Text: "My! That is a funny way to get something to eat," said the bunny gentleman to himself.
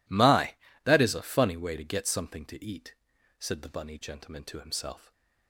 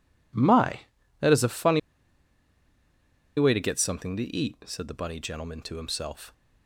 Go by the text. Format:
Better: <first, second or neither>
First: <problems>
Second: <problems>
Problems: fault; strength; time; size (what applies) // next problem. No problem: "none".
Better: first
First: none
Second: pauses between "funny" and "way"; strong; at 1.7 s; 1.5 s long